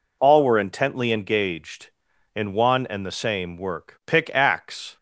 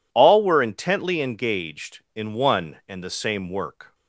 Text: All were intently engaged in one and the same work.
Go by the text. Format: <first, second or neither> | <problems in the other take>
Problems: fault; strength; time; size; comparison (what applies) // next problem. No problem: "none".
second | goes on to say "Pick axe"; noticeable; from 4.0 s on; 0.92 s long